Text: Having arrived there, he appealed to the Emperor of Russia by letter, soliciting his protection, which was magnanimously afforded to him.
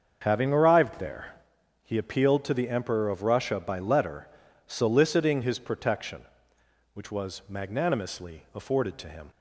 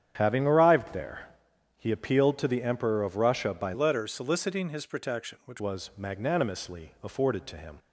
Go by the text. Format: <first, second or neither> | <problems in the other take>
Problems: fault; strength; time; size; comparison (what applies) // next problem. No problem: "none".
first | starts louder than the rest; strong; until 1.1 s; 9 dB; also in the first // changes voice from "letter" to "which"; from 3.7 to 5.5 s; 1.8 s long